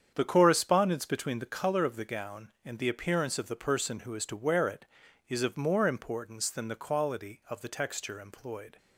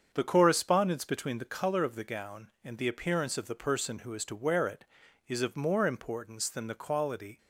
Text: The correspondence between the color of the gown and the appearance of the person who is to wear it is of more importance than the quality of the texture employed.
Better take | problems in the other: first | starts louder than the rest; strong; until 1.1 s; 7 dB; strong in the first // stops before "of the texture employed"; at 7.3 s

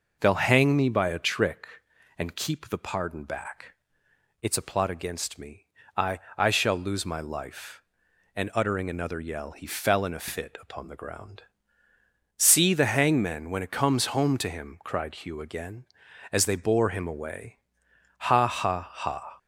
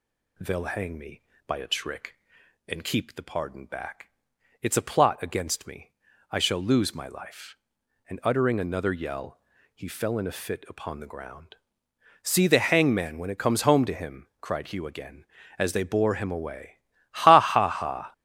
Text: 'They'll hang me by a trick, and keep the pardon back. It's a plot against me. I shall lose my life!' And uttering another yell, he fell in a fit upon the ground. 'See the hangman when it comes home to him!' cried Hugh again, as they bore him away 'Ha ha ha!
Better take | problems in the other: second | says "I" twice; at 6.3 s // pauses between "away" and "Ha"; noticeable; at 17.5 s; 0.60 s long; slight in the second

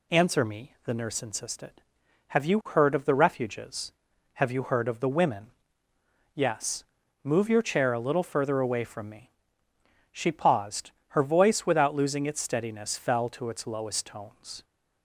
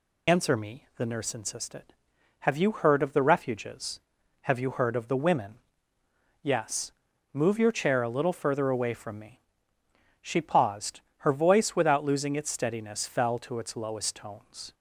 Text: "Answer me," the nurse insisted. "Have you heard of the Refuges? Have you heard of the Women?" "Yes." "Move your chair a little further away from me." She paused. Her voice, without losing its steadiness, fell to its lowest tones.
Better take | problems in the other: first | loses the start of "Answer"; at 0.2 s; 50 ms

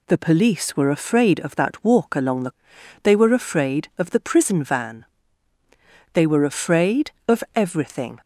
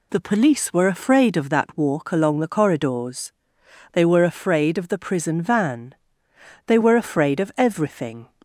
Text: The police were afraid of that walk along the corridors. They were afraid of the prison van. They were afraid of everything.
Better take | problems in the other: second | skips "corridors"; at 2.7 s

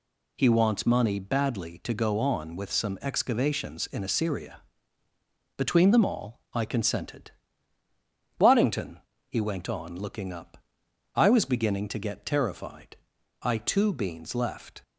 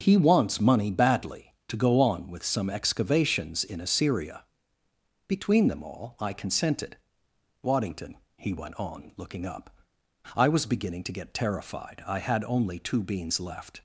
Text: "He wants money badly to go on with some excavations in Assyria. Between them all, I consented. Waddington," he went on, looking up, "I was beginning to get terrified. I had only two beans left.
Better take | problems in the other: second | skips "had only"; at 13.5 s

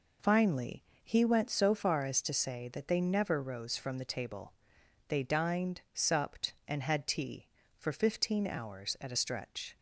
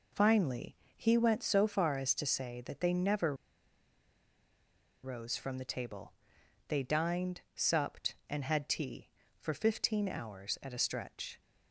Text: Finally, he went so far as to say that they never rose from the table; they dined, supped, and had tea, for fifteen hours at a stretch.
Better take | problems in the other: first | pauses between "never" and "rose"; strong; at 3.3 s; 1.7 s long

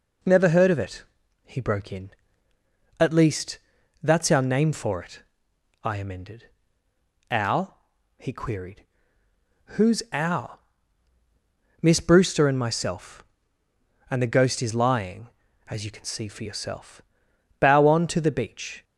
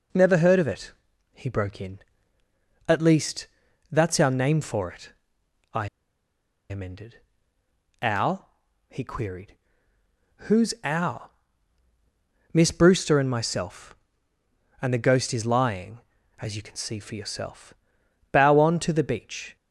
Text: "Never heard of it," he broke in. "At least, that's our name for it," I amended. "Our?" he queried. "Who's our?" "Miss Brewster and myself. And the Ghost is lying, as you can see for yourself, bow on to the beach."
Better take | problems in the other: first | pauses between "I" and "amended"; noticeable; at 5.8 s; 0.83 s long

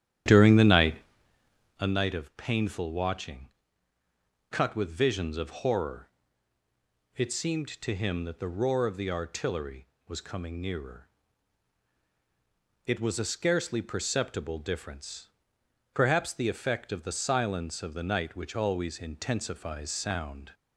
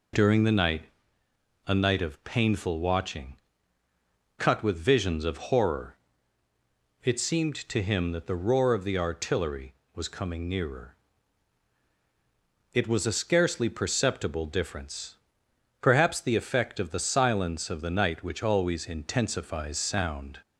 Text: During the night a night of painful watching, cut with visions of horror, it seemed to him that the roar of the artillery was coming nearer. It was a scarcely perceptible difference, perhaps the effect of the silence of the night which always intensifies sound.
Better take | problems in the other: second | starts louder than the rest; strong; until 1.9 s; 11.5 dB // pauses between "night" and "a"; noticeable; at 0.9 s; 0.84 s long; noticeable in the second

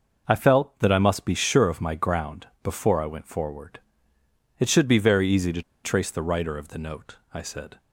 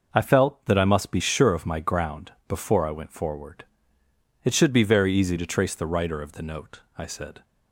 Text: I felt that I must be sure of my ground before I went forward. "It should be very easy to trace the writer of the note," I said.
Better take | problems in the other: second | pauses between "ground" and "before"; slight; at 2.4 s; 0.16 s long; slight in the second // pauses between "to" and "trace"; slight; at 5.6 s; 0.22 s long

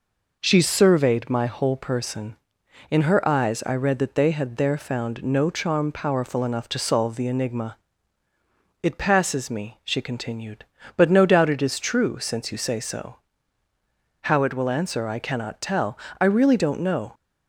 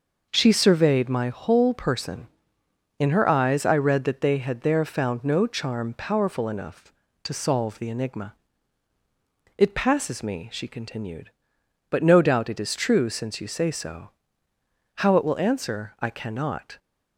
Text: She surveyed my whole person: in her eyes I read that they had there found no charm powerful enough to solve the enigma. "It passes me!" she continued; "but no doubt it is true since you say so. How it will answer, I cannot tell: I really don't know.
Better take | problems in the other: first | stops before "tell I really don't know"; at 16.7 s

